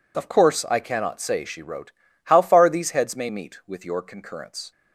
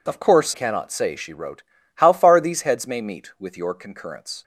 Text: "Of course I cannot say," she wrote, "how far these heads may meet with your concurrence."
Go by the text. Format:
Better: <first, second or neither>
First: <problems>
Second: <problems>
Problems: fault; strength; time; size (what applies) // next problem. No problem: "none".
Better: first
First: none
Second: skips "I"; at 0.5 s